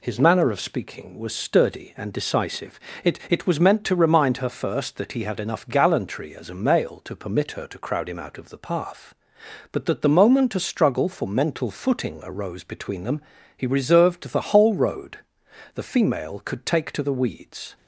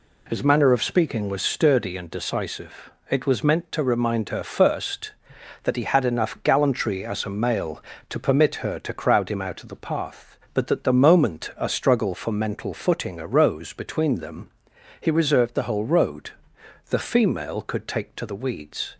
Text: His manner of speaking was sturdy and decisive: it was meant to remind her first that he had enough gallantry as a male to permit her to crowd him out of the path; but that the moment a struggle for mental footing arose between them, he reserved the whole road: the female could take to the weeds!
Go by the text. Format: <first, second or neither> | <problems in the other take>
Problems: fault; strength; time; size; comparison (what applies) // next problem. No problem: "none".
second | says "it" twice; at 3.2 s